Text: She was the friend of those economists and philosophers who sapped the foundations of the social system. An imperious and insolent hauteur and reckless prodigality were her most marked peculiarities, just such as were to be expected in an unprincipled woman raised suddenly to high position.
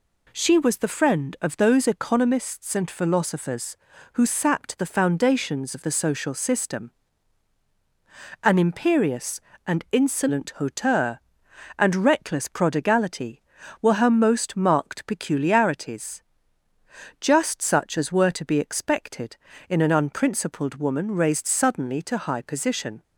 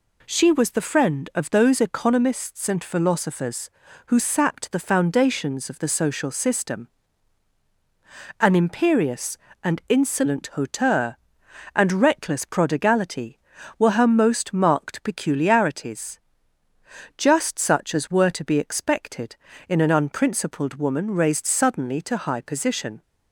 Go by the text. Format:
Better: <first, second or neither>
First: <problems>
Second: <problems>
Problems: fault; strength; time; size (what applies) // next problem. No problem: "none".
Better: neither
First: none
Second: none